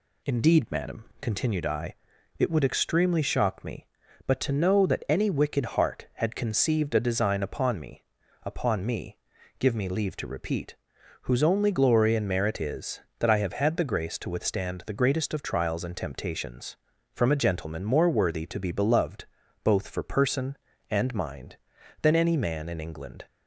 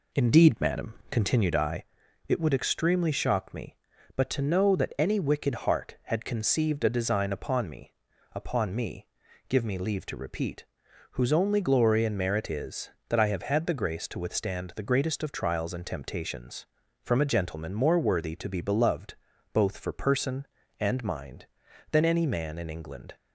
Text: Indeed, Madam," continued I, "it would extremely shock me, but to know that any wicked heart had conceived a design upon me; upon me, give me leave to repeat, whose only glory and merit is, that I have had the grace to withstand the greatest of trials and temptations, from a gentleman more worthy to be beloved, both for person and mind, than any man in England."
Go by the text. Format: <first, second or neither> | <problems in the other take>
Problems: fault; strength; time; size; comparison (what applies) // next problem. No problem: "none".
first | starts louder than the rest; slight; until 1.9 s; 2.5 dB